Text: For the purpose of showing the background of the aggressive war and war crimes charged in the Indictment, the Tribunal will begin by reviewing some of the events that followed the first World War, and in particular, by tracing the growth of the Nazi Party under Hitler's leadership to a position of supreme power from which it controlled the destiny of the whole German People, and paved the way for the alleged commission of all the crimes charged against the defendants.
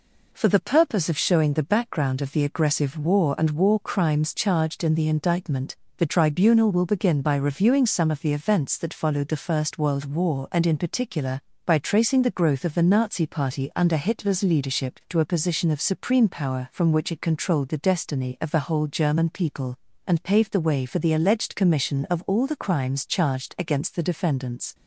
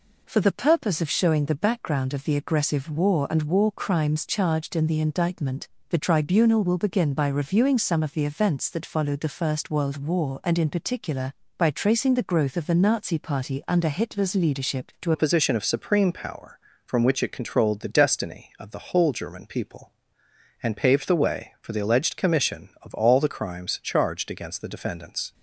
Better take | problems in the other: first | changes voice at "a"; from 15.1 s on; 10.2 s long

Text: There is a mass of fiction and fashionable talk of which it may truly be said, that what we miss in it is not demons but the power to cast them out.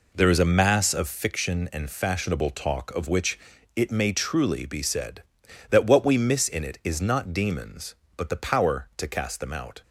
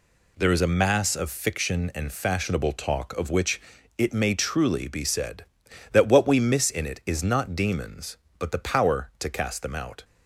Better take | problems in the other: second | starts louder than the rest; until 1.2 s; 3.5 dB // pauses between "which" and "it"; slight; at 3.3 s; 0.36 s long; slight in the second

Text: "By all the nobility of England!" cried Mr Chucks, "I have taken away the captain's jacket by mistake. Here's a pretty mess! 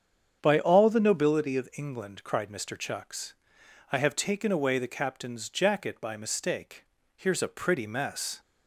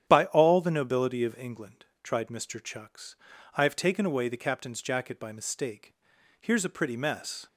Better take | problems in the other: first | starts louder than the rest; strong; until 1.1 s; 9.5 dB; strong in the first // says "tried" for "cried"; at 2.0 s

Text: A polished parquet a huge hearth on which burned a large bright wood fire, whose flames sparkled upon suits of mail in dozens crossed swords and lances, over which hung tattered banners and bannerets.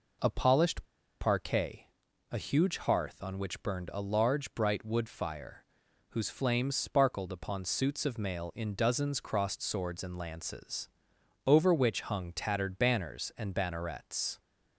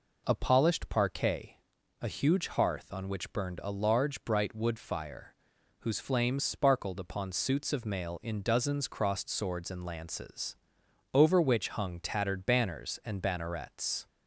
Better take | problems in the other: second | pauses between "polished" and "parquet"; at 0.8 s; 0.36 s long // pauses between "parquet" and "a"; at 1.8 s; 0.44 s long; also in the second

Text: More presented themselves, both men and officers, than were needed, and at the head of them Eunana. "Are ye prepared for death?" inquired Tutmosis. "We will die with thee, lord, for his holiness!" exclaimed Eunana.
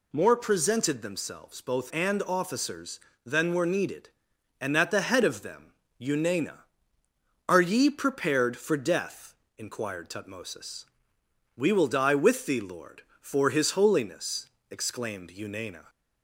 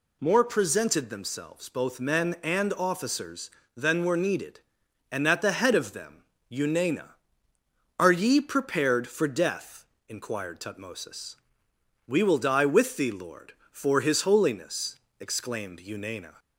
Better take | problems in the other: second | skips "men"; at 1.9 s // pauses between "them" and "Eunana"; slight; at 5.7 s; 0.28 s long; slight in the second

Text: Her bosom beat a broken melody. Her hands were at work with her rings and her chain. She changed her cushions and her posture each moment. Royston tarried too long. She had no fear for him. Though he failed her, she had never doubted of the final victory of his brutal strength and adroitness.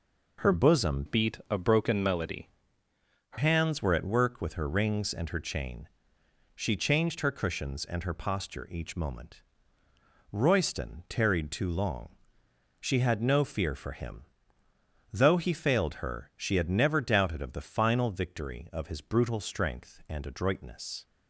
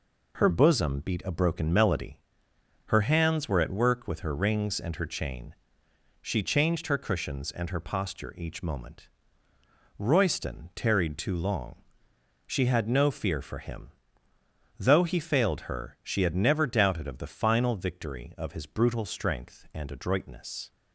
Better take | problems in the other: second | changes voice from "beat" to "Her"; from 1.0 to 3.3 s; 2.3 s long

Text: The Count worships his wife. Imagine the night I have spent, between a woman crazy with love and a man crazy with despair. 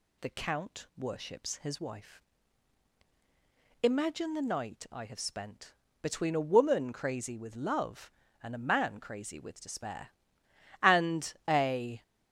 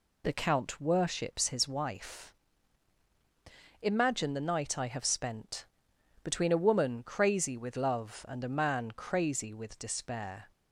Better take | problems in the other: second | goes on to say "And a"; noticeable; from 10.8 s on; 1.2 s long

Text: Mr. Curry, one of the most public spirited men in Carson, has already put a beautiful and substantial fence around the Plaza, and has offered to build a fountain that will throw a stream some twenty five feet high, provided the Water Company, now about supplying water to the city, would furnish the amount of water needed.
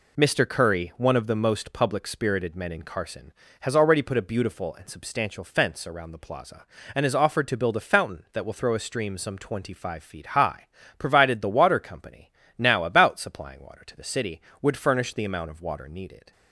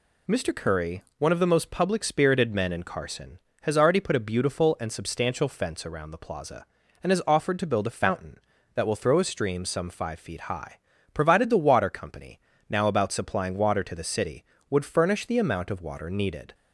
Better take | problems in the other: first | skips "twenty"; at 9.8 s

